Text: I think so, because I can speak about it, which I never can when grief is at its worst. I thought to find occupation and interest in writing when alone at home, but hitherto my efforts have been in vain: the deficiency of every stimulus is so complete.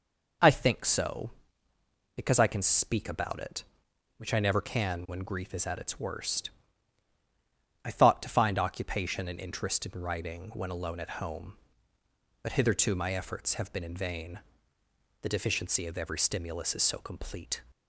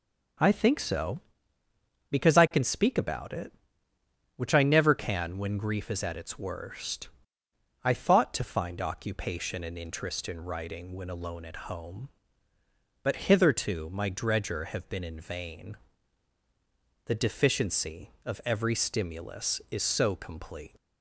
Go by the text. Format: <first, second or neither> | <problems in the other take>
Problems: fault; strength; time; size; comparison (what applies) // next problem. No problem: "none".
first | says "dredger" for "efforts"; at 14.0 s